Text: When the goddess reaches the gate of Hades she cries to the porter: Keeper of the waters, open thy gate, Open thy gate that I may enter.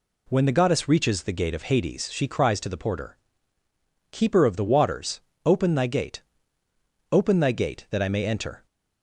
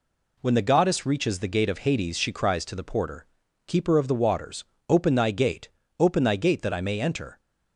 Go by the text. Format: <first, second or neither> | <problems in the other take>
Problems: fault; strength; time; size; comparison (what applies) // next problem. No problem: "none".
neither | none